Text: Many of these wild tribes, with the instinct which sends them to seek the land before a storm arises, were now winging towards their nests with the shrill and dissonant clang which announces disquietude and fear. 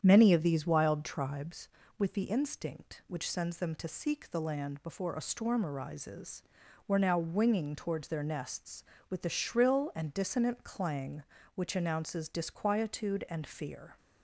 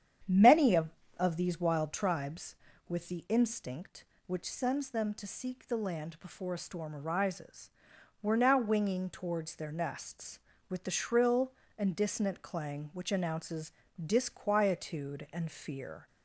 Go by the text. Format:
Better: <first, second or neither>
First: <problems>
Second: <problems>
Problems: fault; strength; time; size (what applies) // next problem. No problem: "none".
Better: first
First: starts louder than the rest; strong; until 1.0 s; 8.5 dB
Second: starts louder than the rest; strong; until 1.5 s; 9 dB // says "of" twice; at 1.1 s // pauses between "announces" and "disquietude"; slight; at 13.7 s; 0.34 s long